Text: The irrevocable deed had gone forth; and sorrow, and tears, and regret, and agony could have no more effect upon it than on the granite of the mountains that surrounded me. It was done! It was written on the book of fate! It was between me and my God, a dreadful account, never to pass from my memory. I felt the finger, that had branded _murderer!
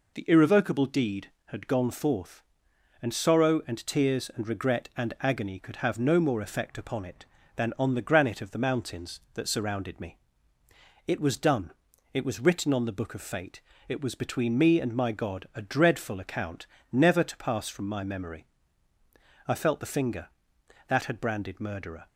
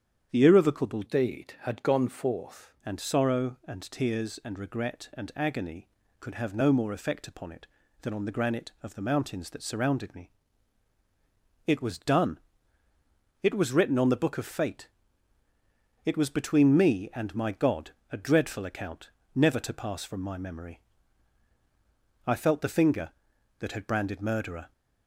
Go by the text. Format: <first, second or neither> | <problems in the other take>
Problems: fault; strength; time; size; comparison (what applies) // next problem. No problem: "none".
first | starts louder than the rest; strong; until 1.3 s; 8.5 dB // changes voice from "deed" to "forth"; from 1.0 to 2.7 s; 1.7 s long